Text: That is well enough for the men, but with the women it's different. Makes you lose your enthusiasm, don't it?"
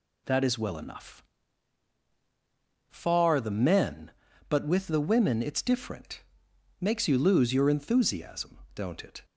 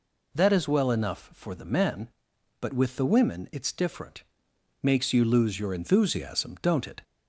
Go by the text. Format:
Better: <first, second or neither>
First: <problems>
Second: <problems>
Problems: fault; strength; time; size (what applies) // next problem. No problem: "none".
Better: second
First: says "far" for "for"; at 2.8 s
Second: none